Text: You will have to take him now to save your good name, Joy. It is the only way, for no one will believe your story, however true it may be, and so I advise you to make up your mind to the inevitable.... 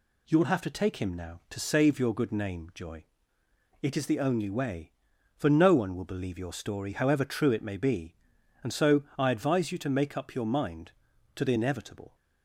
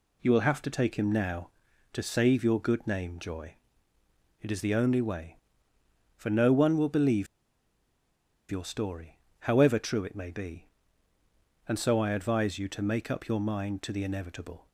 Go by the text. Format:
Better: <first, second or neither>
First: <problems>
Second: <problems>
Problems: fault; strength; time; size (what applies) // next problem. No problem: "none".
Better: first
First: none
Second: pauses between "believe" and "your"; strong; at 7.2 s; 1.2 s long